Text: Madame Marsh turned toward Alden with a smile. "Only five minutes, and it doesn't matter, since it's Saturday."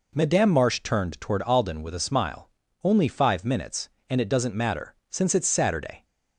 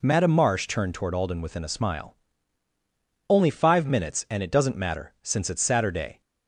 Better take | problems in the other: first | says "within" for "with"; at 1.4 s

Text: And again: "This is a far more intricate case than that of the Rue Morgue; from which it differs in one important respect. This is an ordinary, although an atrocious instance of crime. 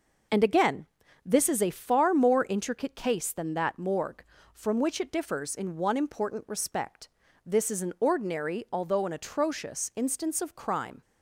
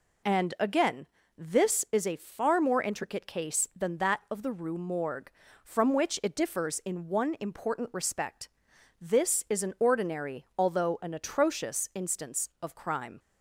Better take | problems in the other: second | skips "of the Rue"; at 3.7 s

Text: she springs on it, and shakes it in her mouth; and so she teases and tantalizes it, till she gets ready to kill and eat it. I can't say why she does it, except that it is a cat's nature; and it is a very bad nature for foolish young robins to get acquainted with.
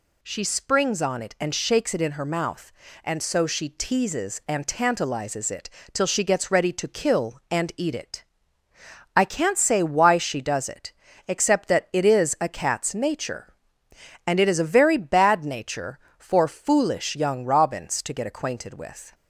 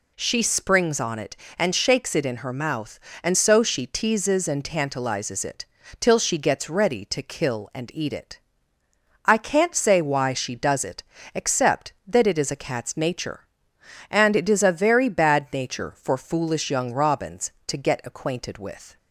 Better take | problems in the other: neither | none

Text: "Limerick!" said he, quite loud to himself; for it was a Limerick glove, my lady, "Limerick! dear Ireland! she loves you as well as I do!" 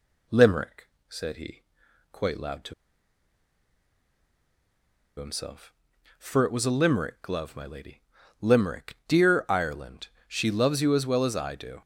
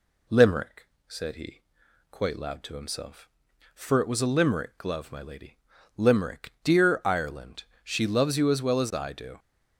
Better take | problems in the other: second | pauses between "to" and "himself"; strong; at 2.7 s; 2.4 s long

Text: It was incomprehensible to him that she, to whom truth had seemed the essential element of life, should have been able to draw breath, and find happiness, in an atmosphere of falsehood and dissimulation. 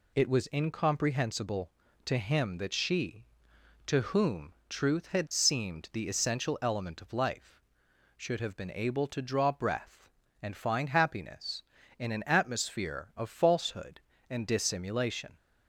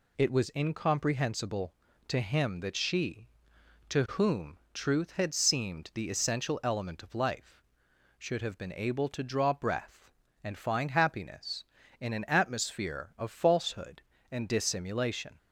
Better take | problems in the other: neither | pauses between "whom" and "truth"; slight; the same in both

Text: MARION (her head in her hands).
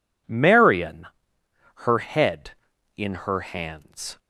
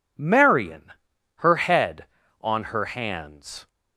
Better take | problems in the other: first | says "on" for "in"; at 2.4 s

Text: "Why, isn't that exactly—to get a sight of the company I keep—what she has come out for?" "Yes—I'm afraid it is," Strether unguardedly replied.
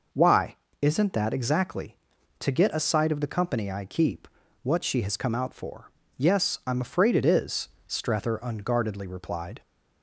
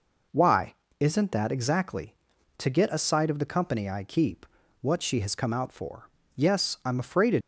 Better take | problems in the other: first | stops before "is Strether unguardedly replied"; at 7.4 s

